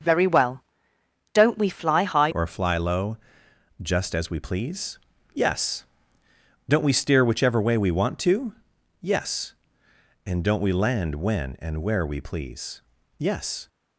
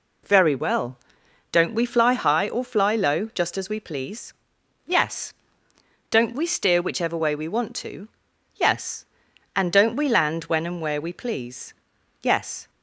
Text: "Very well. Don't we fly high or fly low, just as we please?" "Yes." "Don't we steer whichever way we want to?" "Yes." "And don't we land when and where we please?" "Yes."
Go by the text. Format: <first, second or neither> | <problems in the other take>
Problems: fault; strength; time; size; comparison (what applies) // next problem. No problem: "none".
second | starts louder than the rest; until 1.7 s; 6 dB // changes voice at "or"; from 2.2 s on; 11.4 s long